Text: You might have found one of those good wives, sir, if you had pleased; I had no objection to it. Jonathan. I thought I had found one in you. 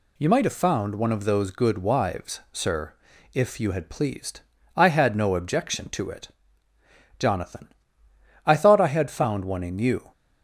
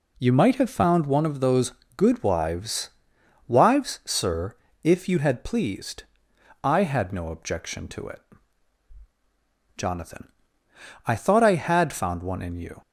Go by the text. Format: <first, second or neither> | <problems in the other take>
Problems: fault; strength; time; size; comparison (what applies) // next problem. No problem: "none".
first | pauses between "those" and "good"; slight; at 1.7 s; 0.24 s long // says "wives" twice; at 3.4 s